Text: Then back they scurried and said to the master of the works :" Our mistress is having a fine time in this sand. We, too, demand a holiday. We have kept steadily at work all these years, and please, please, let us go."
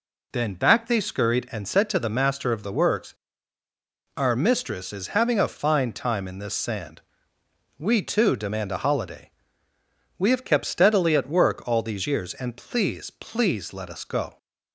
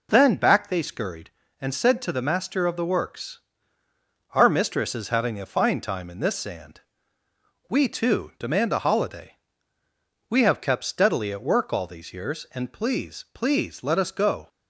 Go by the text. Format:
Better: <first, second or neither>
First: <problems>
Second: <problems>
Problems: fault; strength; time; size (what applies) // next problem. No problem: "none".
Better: neither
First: none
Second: none